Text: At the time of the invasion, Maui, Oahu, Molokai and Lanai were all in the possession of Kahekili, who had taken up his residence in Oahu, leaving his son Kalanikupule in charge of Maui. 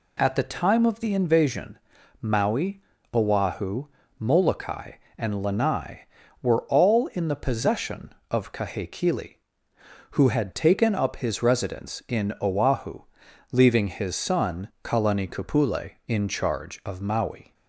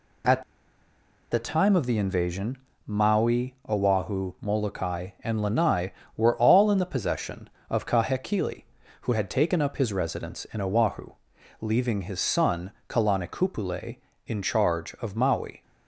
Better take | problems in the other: first | pauses between "At" and "the"; noticeable; at 0.4 s; 0.89 s long // pauses between "son" and "Kalanikupule"; slight; at 12.7 s; 0.16 s long; slight in the first

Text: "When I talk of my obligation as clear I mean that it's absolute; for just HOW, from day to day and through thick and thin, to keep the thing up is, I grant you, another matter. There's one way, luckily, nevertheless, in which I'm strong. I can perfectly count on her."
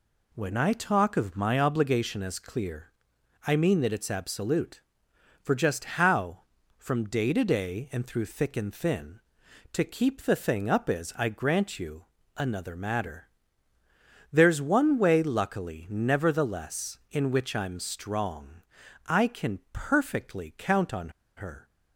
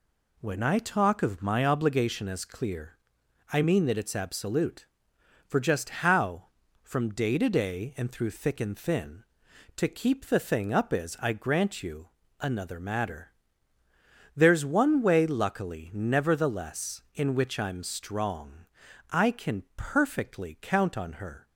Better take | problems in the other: second | pauses between "clear" and "I"; noticeable; at 2.8 s; 0.56 s long; noticeable in the second // pauses between "on" and "her"; slight; at 21.0 s; 0.27 s long

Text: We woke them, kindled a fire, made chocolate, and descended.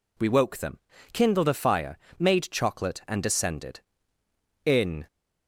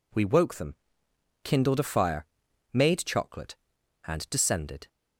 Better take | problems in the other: second | goes on to say "In"; slight; from 4.6 s on; 0.42 s long

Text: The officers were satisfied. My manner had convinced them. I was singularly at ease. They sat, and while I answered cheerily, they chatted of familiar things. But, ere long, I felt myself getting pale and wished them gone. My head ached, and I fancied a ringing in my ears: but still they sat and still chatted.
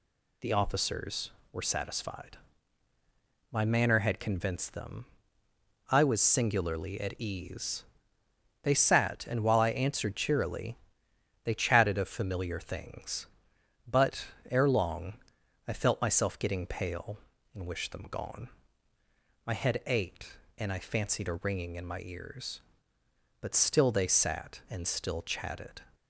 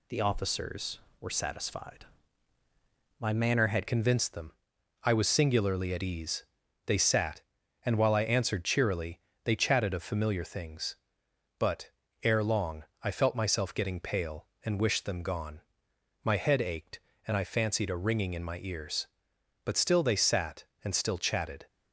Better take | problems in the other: first | changes voice at "convinced"; from 3.8 s on; 17.8 s long

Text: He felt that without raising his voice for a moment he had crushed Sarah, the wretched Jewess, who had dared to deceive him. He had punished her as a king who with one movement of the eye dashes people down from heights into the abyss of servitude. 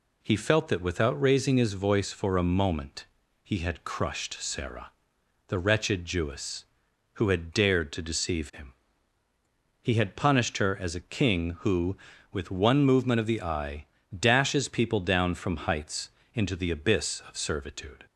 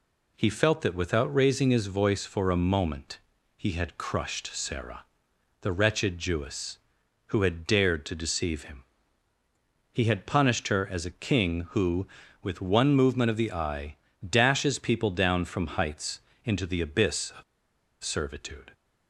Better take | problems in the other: first | pauses between "moment" and "he"; at 3.1 s; 0.38 s long; also in the first // pauses between "eye" and "dashes"; slight; at 13.9 s; 0.32 s long; slight in the first // pauses between "heights" and "into"; slight; at 16.1 s; 0.24 s long; slight in the first // pauses between "of" and "servitude"; noticeable; at 17.4 s; 0.59 s long

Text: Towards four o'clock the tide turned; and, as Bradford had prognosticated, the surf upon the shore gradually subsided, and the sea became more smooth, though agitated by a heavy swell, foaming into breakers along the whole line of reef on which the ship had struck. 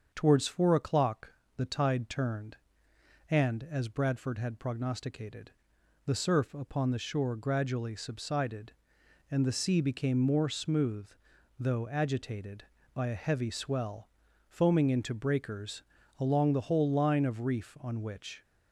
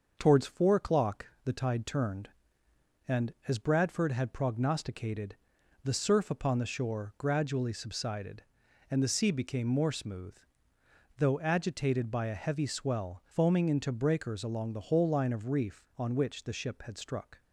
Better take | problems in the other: second | starts louder than the rest; strong; until 1.1 s; 7 dB; also in the second // pauses between "o'clock" and "the"; slight; at 1.3 s; 0.24 s long; slight in the second // pauses between "breakers" and "along"; slight; at 15.8 s; 0.36 s long // stops before "the ship had struck"; at 18.4 s

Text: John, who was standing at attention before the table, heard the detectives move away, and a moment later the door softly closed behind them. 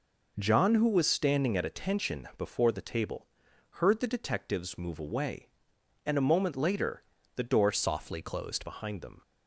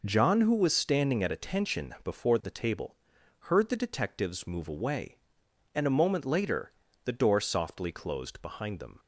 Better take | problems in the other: second | pauses between "later" and "the"; slight; at 7.0 s; 0.34 s long; slight in the second // changes voice from "softly" to "closed"; from 7.7 to 8.6 s; 0.9 s long

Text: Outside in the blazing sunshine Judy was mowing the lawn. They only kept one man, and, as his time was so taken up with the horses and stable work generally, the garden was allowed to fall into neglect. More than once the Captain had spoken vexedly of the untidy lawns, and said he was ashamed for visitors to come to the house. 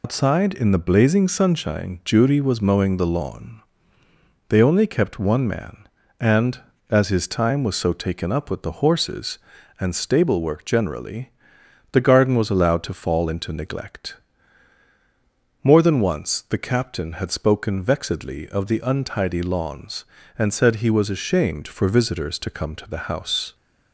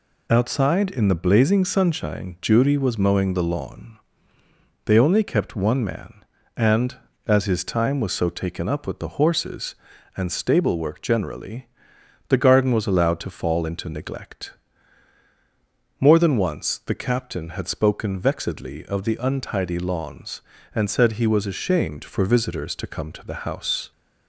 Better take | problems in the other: second | loses the start of "Outside"; at 0.0 s; 115 ms

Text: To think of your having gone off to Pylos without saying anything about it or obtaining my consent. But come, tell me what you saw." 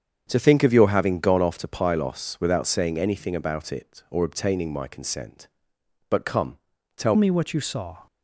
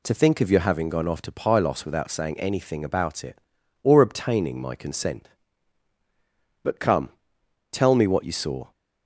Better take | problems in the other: second | starts louder than the rest; strong; until 1.2 s; 7.5 dB // changes voice at "me"; from 7.1 s on; 0.9 s long

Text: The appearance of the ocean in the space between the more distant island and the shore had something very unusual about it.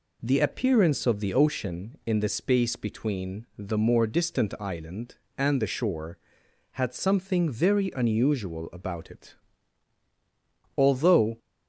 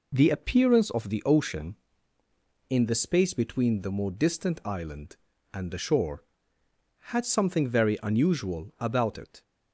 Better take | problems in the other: second | goes on to say "Although"; from 10.7 s on; 0.60 s long

